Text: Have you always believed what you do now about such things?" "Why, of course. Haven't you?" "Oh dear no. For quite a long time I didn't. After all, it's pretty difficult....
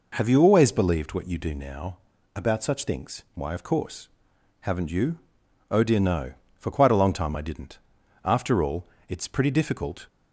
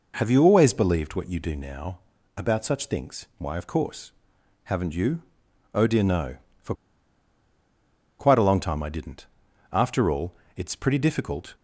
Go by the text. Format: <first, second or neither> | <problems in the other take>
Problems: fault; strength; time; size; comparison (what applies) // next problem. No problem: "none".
first | pauses between "now" and "about"; at 1.9 s; 0.38 s long; also in the first // pauses between "For" and "quite"; strong; at 6.7 s; 1.4 s long